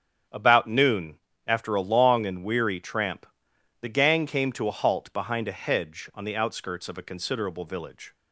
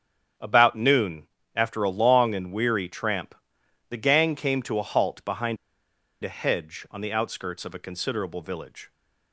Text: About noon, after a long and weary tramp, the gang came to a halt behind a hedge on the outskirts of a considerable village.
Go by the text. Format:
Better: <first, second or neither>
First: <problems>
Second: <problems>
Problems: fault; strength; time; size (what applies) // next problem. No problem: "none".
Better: first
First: starts louder than the rest; strong; until 1.5 s; 8.5 dB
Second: starts louder than the rest; strong; until 1.6 s; 8.5 dB // pauses between "behind" and "a"; noticeable; at 5.5 s; 0.66 s long